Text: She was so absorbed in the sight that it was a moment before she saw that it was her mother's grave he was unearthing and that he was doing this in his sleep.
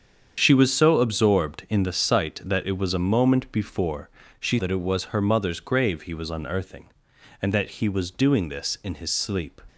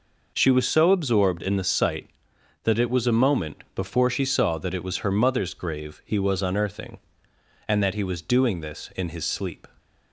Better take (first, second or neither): second